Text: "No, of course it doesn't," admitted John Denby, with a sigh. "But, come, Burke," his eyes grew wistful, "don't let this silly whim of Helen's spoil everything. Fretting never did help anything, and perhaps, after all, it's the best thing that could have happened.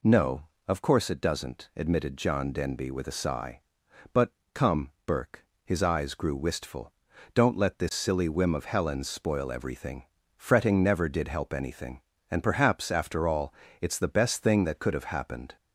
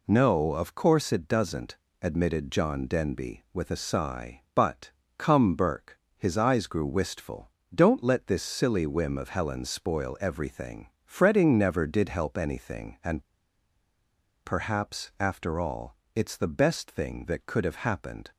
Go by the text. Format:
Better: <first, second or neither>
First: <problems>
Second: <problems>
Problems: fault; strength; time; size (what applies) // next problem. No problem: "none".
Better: first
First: none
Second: pauses between "and" and "perhaps"; at 13.2 s; 1.2 s long